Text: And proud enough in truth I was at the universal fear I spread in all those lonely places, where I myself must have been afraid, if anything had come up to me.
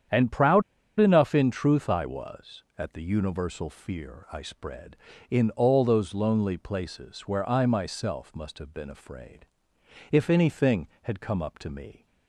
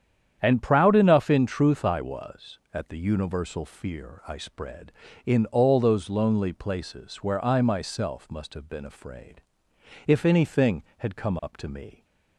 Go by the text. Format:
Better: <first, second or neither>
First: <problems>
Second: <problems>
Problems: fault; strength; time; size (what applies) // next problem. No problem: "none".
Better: second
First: starts louder than the rest; strong; until 1.4 s; 9 dB // pauses between "proud" and "enough"; at 0.6 s; 0.37 s long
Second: starts louder than the rest; strong; until 1.4 s; 9 dB